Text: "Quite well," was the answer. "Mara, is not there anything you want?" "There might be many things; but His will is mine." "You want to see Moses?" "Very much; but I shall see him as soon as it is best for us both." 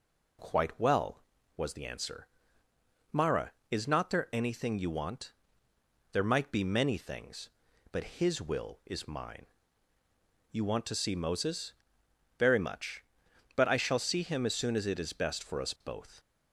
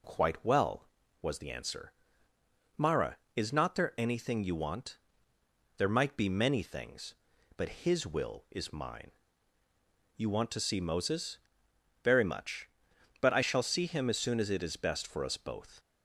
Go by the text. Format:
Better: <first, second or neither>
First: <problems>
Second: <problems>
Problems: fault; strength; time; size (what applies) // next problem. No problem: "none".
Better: neither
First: none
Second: none